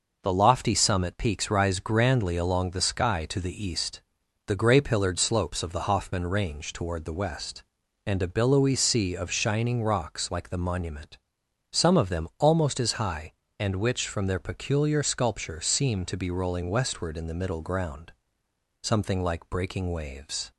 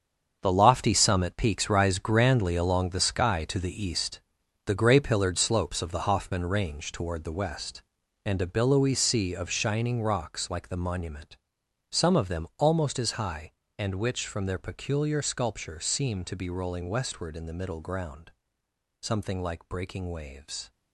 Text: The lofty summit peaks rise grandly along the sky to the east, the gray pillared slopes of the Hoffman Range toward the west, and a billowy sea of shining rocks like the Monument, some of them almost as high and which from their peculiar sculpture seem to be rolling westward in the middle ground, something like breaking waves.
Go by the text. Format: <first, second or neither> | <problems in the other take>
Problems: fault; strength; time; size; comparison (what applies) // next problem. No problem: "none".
first | gets quieter; strong; throughout; 11 dB